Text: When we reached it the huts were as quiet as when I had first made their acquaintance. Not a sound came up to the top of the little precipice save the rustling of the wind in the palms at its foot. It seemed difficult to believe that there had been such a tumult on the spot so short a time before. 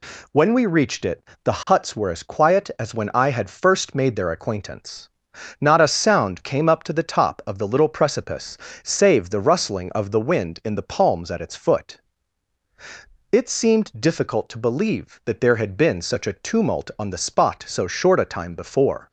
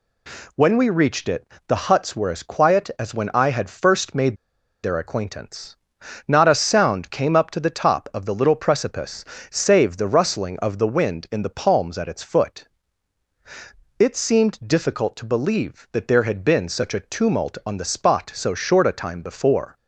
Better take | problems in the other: first | pauses between "it" and "the"; slight; at 1.4 s; 0.22 s long; slight in the first // pauses between "made" and "their"; noticeable; at 4.3 s; 0.48 s long // pauses between "precipice" and "save"; slight; at 9.2 s; 0.26 s long; slight in the first

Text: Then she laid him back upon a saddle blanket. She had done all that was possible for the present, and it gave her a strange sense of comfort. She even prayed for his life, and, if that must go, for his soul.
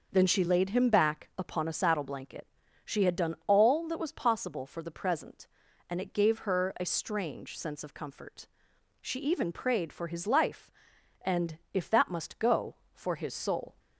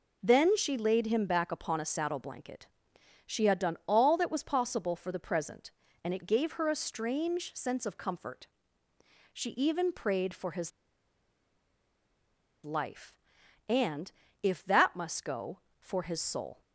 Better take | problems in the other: first | pauses between "his" and "life"; strong; at 10.7 s; 1.9 s long

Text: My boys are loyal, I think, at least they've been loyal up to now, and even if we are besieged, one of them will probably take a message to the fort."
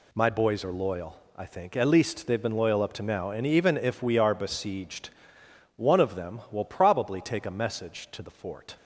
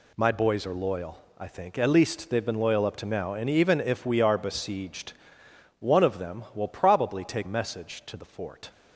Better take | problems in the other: first | skips "a"; at 7.4 s

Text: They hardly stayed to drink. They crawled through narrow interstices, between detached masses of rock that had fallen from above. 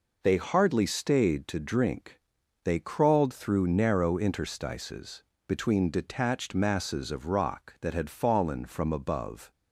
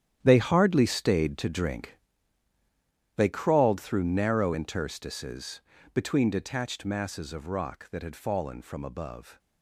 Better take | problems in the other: first | gets quieter; strong; throughout; 12.5 dB

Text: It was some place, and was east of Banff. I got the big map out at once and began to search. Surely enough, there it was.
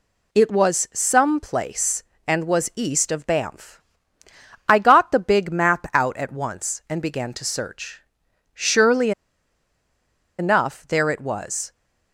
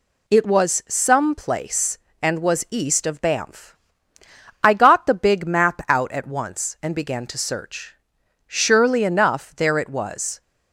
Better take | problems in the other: second | pauses between "Surely" and "enough"; strong; at 9.1 s; 1.2 s long

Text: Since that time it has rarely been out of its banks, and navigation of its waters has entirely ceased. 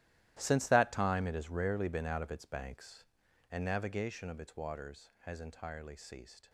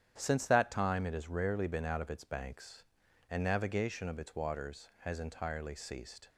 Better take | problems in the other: second | gets quieter; strong; throughout; 16 dB // starts louder than the rest; strong; until 1.4 s; 14.5 dB; strong in the second

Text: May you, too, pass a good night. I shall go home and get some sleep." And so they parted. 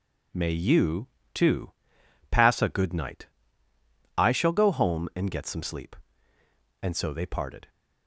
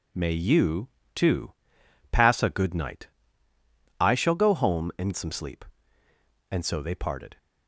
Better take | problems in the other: first | skips "get"; at 5.1 s

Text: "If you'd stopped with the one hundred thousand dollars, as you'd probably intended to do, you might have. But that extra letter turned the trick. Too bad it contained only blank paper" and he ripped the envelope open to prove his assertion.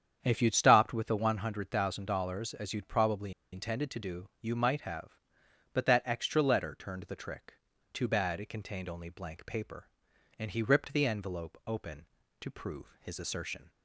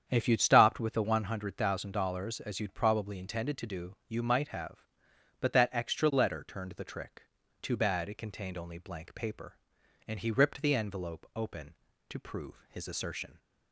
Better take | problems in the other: second | starts louder than the rest; strong; until 1.2 s; 8 dB; strong in the second // pauses between "probably" and "intended"; slight; at 3.3 s; 0.20 s long

